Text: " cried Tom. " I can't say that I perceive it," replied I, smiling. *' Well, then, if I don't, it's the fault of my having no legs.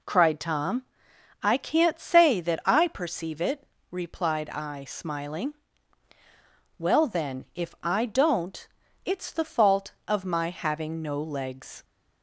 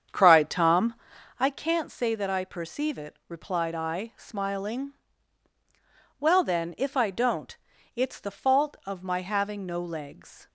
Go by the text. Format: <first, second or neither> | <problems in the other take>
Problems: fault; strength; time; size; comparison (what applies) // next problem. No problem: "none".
first | starts louder than the rest; strong; until 1.6 s; 7.5 dB